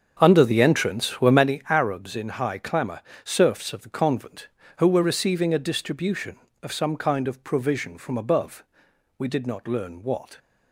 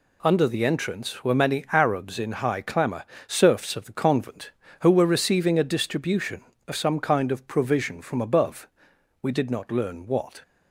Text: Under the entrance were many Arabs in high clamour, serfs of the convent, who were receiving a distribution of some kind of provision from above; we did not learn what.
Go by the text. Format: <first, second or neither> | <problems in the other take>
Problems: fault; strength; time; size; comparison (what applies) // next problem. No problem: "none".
second | starts louder than the rest; strong; until 1.5 s; 7 dB